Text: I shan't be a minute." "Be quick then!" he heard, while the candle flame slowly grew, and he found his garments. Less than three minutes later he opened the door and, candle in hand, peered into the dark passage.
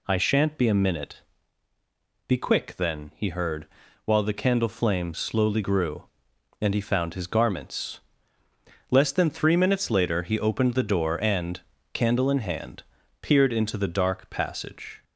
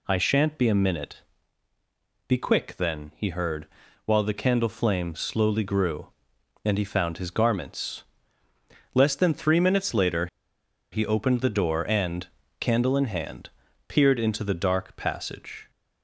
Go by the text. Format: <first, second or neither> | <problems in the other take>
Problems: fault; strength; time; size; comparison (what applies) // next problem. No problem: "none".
first | pauses between "later" and "he"; noticeable; at 10.2 s; 0.65 s long